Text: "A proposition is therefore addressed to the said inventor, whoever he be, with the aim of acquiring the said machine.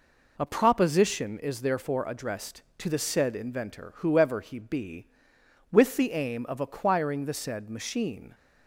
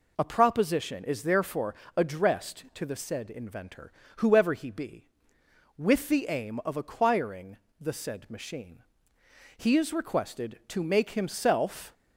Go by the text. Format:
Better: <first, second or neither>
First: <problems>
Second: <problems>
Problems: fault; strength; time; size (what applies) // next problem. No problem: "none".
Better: first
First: none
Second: pauses between "therefore" and "addressed"; slight; at 1.7 s; 0.22 s long // pauses between "acquiring" and "the"; slight; at 7.5 s; 0.24 s long // goes on to say "He is requested to make himself"; strong; from 9.5 s on; 2.3 s long